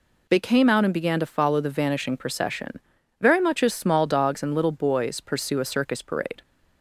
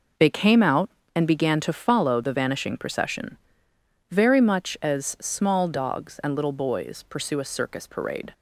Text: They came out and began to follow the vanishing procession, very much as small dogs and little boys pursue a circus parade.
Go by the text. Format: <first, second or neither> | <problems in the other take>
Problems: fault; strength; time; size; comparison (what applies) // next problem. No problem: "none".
neither | none